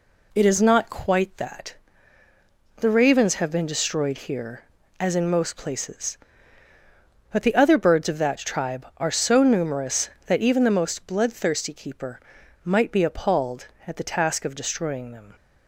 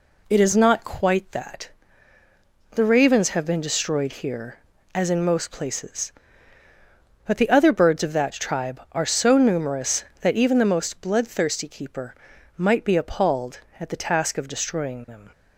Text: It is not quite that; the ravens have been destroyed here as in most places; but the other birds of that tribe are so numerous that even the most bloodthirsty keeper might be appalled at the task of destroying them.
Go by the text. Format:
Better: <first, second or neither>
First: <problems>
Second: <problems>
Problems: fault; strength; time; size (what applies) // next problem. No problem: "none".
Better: neither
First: pauses between "keeper" and "might"; at 12.2 s; 0.43 s long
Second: pauses between "keeper" and "might"; at 12.1 s; 0.42 s long